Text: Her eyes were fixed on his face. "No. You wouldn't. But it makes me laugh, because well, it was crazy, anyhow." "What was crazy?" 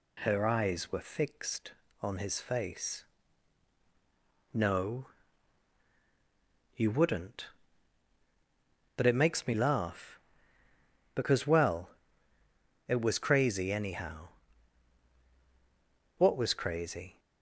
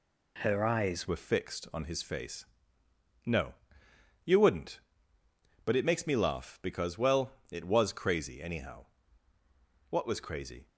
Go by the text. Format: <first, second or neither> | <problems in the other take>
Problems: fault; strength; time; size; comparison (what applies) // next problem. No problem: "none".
first | changes voice at "were"; from 1.0 s on; 9.6 s long